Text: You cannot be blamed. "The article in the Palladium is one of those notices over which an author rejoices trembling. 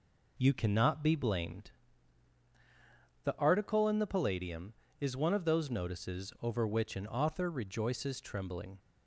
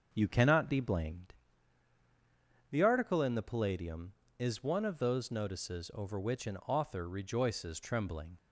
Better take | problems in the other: first | starts louder than the rest; until 1.3 s; 6.5 dB

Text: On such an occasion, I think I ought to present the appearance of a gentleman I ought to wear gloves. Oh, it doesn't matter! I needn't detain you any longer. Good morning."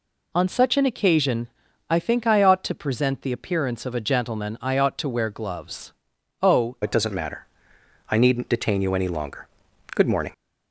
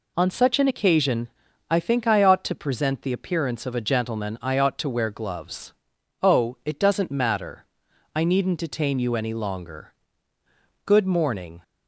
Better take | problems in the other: second | changes voice at "it"; from 6.8 s on; 3.5 s long

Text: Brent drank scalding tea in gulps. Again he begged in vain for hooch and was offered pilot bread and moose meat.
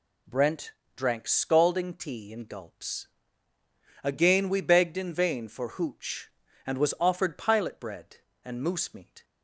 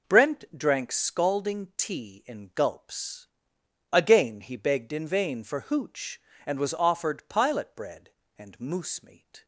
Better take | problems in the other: second | pauses between "Brent" and "drank"; slight; at 0.7 s; 0.24 s long // says "we" for "he"; at 4.4 s

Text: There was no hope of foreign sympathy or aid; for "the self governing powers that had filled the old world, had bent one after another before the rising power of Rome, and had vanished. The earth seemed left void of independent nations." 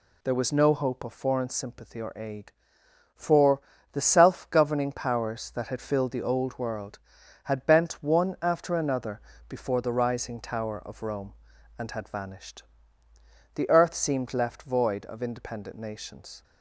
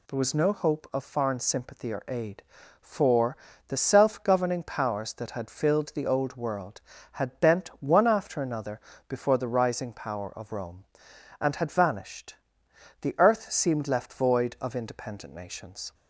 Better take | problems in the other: second | pauses between "for" and "the"; slight; at 3.5 s; 0.34 s long; slight in the second // pauses between "another" and "before"; slight; at 9.2 s; 0.26 s long; slight in the second // says "tower" for "power"; at 10.4 s

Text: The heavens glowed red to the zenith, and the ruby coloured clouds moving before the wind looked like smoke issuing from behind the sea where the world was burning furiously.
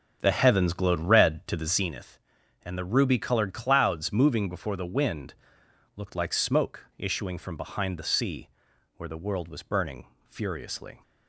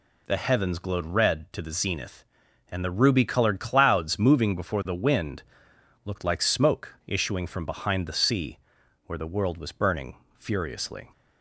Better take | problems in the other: second | starts louder than the rest; until 1.9 s; 6.5 dB // pauses between "wind" and "looked"; noticeable; at 5.3 s; 0.60 s long; noticeable in the second // pauses between "sea" and "where"; noticeable; at 8.4 s; 0.48 s long; noticeable in the second // pauses between "burning" and "furiously"; slight; at 10.0 s; 0.24 s long; slight in the second

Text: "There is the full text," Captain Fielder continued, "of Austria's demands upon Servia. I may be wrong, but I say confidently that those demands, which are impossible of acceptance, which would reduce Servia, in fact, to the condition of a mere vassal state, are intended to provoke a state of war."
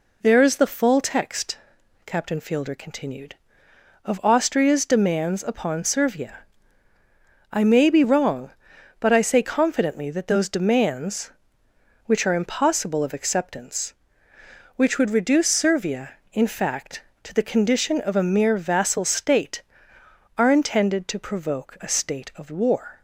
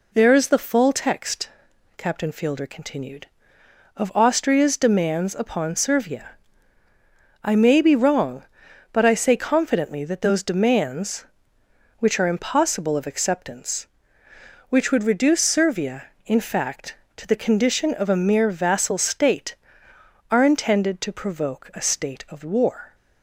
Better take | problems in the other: neither | none

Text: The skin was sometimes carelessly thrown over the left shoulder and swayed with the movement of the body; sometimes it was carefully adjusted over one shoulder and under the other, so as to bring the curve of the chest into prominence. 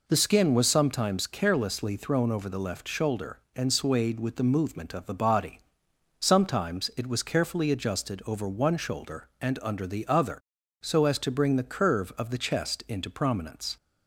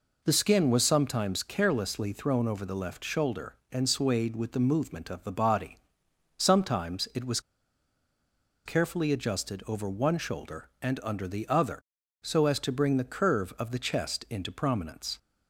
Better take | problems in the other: first | pauses between "was" and "carefully"; strong; at 7.4 s; 1.2 s long

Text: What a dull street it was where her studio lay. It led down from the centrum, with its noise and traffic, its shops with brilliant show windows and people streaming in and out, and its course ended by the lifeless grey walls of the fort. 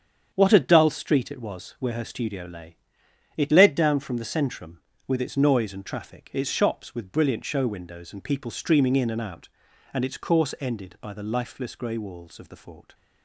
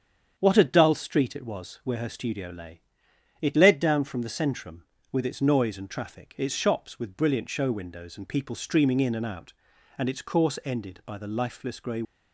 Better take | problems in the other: first | starts louder than the rest; strong; until 1.3 s; 8 dB; strong in the first // stops before "walls of the fort"; at 12.0 s

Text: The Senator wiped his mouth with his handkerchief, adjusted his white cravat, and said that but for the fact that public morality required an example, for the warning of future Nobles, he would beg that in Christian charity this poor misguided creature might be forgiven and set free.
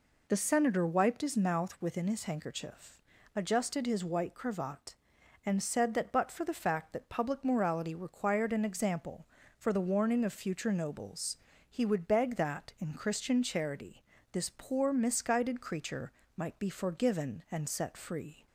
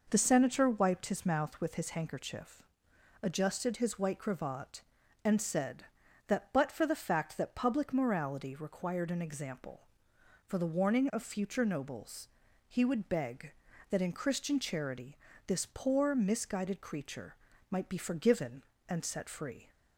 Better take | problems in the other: second | says "within" for "with"; at 1.8 s // pauses between "charity" and "this"; slight; at 14.0 s; 0.30 s long; slight in the second // pauses between "creature" and "might"; slight; at 16.1 s; 0.26 s long; slight in the second

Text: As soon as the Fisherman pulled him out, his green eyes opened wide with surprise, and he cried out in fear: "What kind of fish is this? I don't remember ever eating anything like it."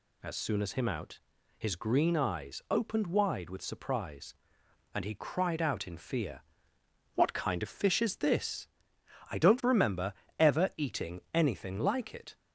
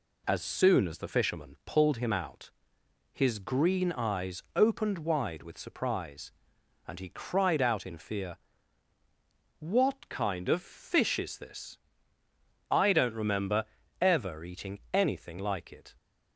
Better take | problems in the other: second | skips "the Fisherman pulled"; at 0.7 s // pauses between "remember" and "ever"; slight; at 10.1 s; 0.26 s long; slight in the second

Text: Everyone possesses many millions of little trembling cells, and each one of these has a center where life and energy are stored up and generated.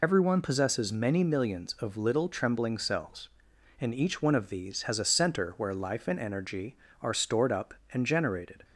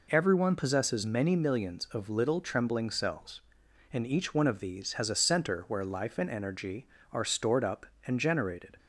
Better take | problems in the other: second | loses the start of "Everyone"; at 0.0 s; 70 ms

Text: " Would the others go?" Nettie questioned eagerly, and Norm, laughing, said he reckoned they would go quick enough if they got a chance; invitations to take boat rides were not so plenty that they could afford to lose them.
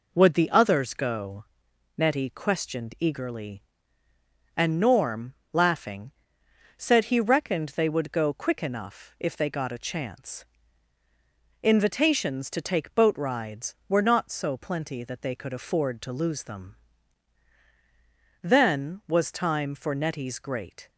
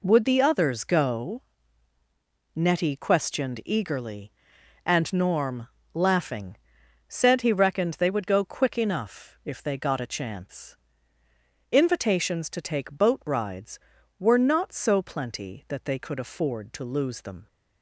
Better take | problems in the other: second | goes on to say "Then was time for Nettie's great"; strong; from 18.4 s on; 2.4 s long

